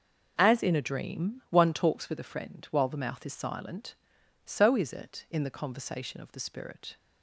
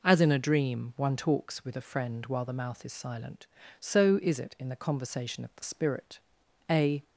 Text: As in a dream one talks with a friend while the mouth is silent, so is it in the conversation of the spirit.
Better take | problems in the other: first | goes on to say "A"; slight; from 6.7 s on; 0.32 s long

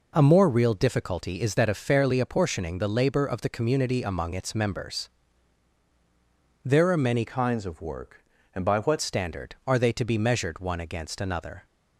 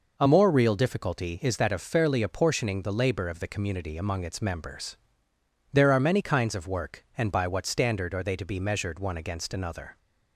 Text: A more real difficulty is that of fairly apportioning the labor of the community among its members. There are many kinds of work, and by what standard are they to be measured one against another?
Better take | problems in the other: second | changes voice from "kinds" to "what"; from 7.2 to 8.9 s; 1.7 s long

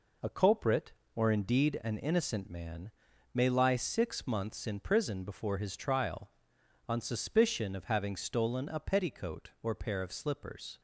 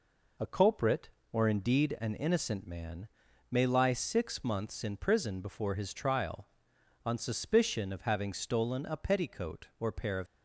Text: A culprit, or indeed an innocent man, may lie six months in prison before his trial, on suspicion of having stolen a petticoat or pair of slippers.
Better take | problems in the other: first | stops before "slippers"; at 10.2 s

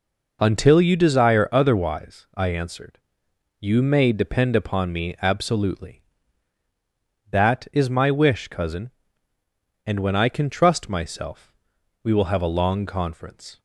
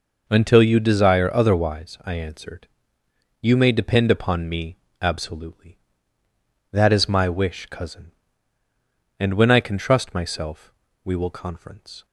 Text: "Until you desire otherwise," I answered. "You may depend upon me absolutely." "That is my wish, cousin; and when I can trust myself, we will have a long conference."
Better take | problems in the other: first | pauses between "me" and "absolutely"; slight; at 4.7 s; 0.22 s long // skips "have a long"; at 11.3 s

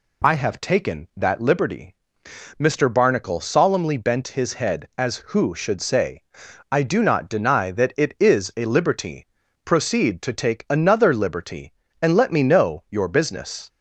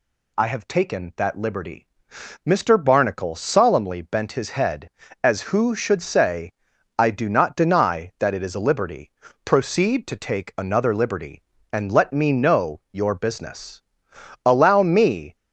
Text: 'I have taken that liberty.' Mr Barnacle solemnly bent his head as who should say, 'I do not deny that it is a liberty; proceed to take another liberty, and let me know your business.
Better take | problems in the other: first | goes on to say "Allow me"; noticeable; from 14.4 s on; 0.92 s long

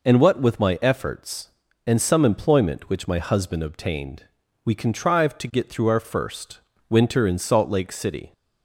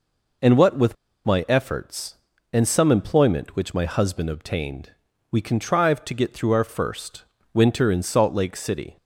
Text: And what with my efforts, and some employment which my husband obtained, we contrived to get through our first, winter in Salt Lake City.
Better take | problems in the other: first | pauses between "with" and "my"; slight; at 0.9 s; 0.31 s long

